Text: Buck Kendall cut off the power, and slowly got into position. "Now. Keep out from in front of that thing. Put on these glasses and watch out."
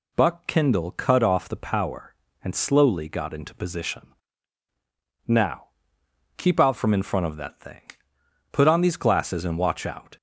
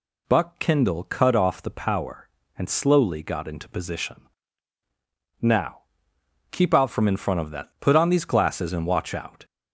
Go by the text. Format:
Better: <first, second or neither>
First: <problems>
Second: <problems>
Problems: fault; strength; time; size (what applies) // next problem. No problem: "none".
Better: first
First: none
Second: skips "thing"; at 7.7 s